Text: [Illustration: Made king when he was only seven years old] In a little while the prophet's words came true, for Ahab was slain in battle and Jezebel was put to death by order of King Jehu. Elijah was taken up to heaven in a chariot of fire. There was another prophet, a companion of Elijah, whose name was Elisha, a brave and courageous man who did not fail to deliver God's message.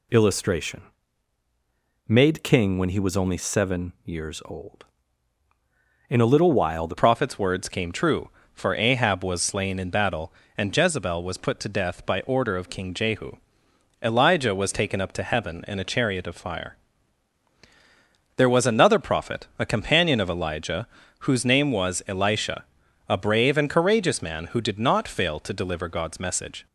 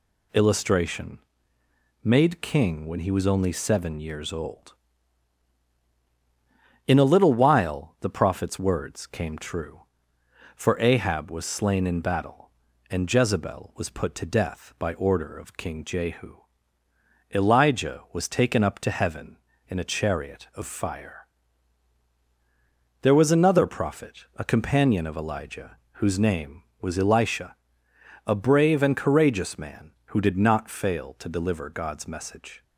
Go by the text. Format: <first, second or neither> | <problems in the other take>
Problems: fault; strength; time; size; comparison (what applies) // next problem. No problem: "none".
second | changes voice at "prophet's"; from 6.9 s on; 19.7 s long